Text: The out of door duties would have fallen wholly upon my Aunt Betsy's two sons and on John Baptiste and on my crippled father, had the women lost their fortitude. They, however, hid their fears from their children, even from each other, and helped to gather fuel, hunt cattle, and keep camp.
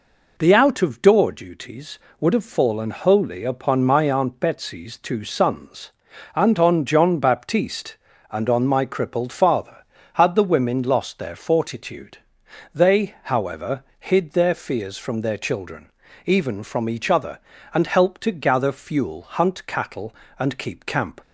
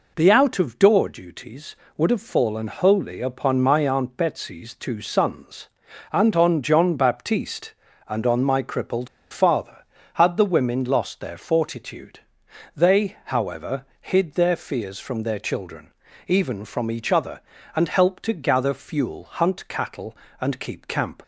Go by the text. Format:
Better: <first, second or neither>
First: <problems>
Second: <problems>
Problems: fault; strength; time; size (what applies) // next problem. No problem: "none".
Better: first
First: none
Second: pauses between "crippled" and "father"; slight; at 9.0 s; 0.24 s long